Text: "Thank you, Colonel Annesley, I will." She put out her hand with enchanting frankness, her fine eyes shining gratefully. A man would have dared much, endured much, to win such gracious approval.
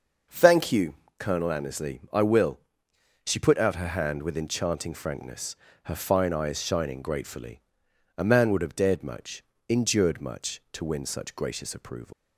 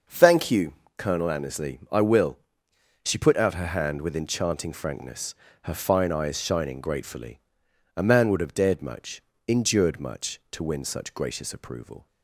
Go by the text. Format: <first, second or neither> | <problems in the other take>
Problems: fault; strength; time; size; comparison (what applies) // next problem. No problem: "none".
second | starts louder than the rest; noticeable; until 1.5 s; 6 dB; noticeable in the second // leaves "approval" unfinished; at 12.1 s; 155 ms